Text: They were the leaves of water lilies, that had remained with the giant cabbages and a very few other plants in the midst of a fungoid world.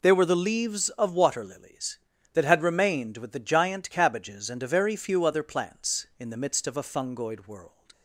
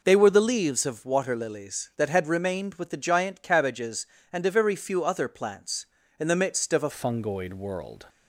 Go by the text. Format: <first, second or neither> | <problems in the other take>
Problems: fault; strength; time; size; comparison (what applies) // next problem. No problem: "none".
first | changes voice at "fungoid"; from 6.9 s on; 1.1 s long